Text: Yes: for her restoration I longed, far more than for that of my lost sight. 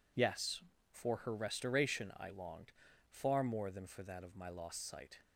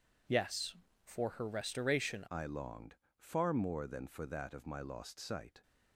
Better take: first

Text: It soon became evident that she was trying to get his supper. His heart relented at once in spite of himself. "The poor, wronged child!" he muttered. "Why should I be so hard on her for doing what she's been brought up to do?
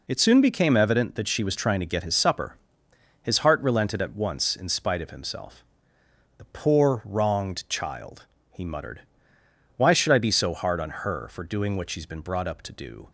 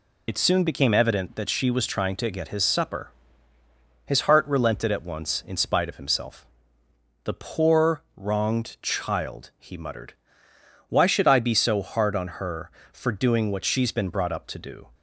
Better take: first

